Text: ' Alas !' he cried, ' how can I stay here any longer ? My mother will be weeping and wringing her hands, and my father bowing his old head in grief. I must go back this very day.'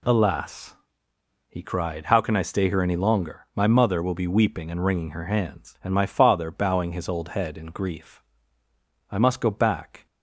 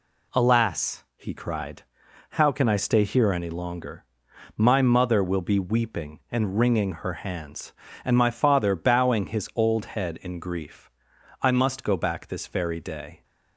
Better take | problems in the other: second | stops before "this very day"; at 10.0 s

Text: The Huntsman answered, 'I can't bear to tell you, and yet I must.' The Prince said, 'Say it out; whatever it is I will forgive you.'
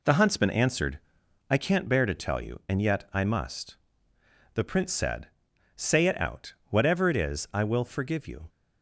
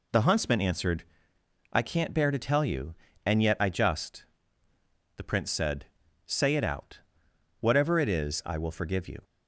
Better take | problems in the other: first | says "just" for "must"; at 3.6 s

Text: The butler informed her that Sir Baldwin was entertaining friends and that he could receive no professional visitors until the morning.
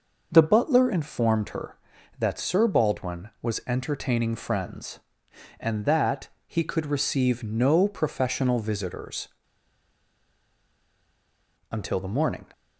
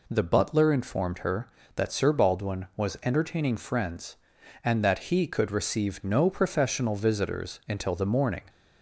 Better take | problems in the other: second | pauses between "that" and "he"; slight; at 6.2 s; 0.18 s long // pauses between "visitors" and "until"; strong; at 9.2 s; 2.4 s long

